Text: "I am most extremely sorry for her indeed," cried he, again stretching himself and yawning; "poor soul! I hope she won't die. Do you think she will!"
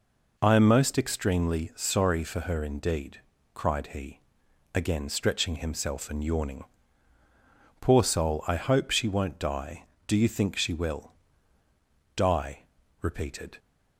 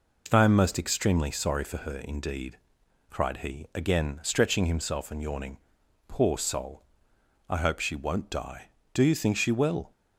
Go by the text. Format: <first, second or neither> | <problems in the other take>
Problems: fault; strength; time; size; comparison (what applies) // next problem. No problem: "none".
second | goes on to say "Die repeated"; from 12.1 s on; 1.4 s long